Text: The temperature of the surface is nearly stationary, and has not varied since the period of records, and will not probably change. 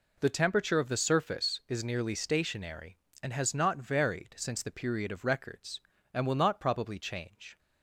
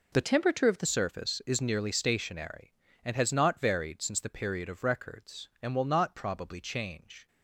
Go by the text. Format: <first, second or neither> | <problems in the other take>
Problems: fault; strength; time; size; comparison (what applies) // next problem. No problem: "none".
first | changes voice from "temperature" to "the"; from 0.2 to 0.8 s; 0.6 s long